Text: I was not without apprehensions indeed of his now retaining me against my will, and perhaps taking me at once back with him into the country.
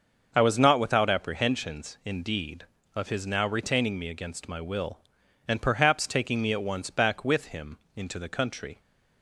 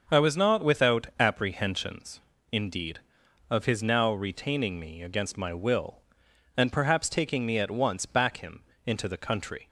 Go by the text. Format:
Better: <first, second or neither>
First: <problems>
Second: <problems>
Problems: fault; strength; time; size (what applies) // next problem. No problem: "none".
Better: first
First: starts louder than the rest; until 1.3 s; 6 dB // pauses between "him" and "into"; slight; at 7.7 s; 0.18 s long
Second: starts louder than the rest; until 1.2 s; 6 dB // pauses between "apprehensions" and "indeed"; slight; at 2.2 s; 0.28 s long // skips "with"; at 8.3 s // pauses between "him" and "into"; slight; at 8.6 s; 0.24 s long